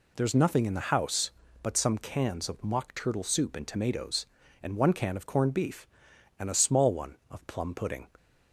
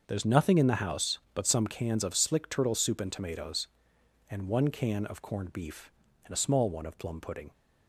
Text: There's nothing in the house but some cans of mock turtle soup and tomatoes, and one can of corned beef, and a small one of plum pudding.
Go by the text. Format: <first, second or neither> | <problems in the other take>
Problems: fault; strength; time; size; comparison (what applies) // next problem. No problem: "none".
first | starts louder than the rest; until 1.0 s; 6.5 dB // says "slick" for "mock"; at 2.1 s